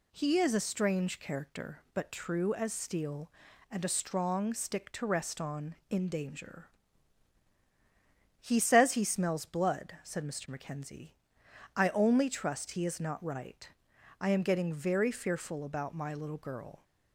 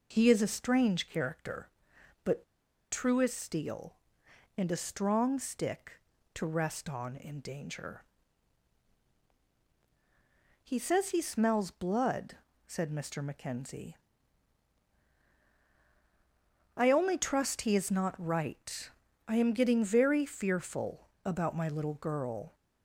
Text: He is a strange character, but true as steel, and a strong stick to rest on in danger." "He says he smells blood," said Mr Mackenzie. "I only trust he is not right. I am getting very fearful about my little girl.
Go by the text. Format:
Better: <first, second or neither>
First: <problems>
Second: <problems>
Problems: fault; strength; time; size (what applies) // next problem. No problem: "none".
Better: first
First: none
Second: pauses between "but" and "true"; noticeable; at 2.4 s; 0.48 s long // pauses between "fearful" and "about"; slight; at 21.0 s; 0.16 s long